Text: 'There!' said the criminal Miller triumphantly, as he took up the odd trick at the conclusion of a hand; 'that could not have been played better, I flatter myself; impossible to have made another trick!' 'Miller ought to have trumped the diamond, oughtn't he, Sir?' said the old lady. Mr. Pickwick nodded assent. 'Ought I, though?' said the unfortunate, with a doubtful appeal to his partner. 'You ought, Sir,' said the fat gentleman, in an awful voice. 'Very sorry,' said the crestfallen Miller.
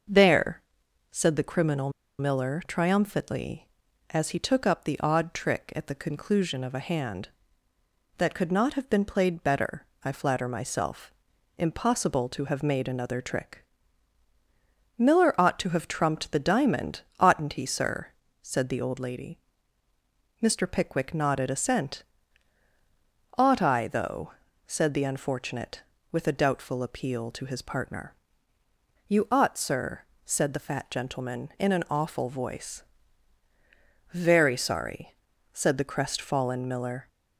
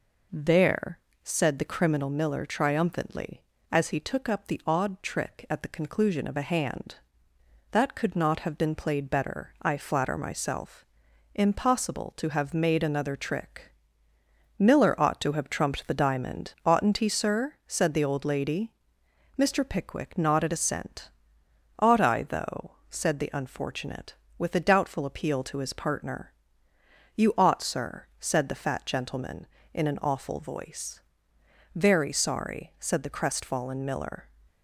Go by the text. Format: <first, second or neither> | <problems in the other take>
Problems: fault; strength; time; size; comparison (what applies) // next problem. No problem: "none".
second | starts louder than the rest; noticeable; until 1.5 s; 6 dB // pauses between "criminal" and "Miller"; slight; at 1.9 s; 0.28 s long